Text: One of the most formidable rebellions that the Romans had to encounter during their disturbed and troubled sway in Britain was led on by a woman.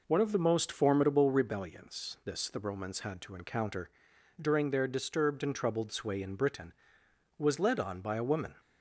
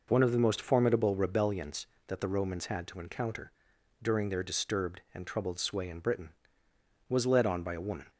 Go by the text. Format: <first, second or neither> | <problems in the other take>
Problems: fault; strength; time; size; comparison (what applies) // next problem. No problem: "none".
second | says "this" for "that"; at 2.2 s // pauses between "encounter" and "during"; noticeable; at 3.8 s; 0.50 s long; noticeable in the second